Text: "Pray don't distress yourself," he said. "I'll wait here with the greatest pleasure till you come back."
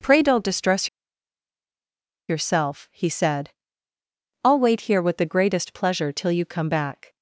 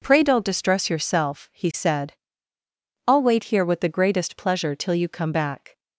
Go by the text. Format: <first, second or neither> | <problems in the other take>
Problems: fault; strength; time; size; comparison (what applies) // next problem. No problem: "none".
second | pauses between "distress" and "yourself"; strong; at 0.8 s; 1.4 s long